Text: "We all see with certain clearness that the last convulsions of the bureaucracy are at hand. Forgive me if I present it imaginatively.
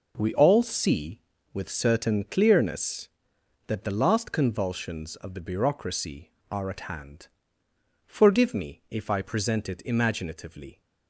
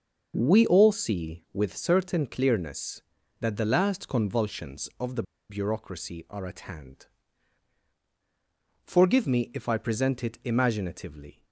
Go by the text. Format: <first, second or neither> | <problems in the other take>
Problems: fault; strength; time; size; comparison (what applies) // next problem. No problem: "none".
first | starts louder than the rest; noticeable; until 1.3 s; 6 dB // pauses between "the" and "bureaucracy"; slight; at 5.2 s; 0.26 s long